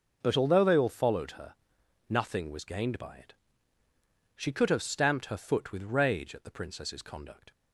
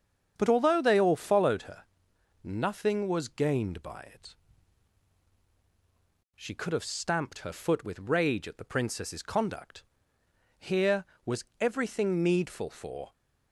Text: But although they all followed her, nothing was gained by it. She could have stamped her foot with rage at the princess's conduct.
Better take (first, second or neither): first